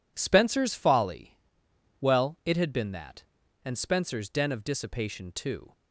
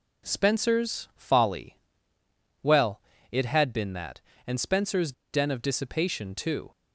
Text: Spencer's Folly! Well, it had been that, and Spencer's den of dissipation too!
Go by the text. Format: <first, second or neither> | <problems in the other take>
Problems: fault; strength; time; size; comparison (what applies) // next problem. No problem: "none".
first | pauses between "Spencer's" and "den"; slight; at 5.1 s; 0.19 s long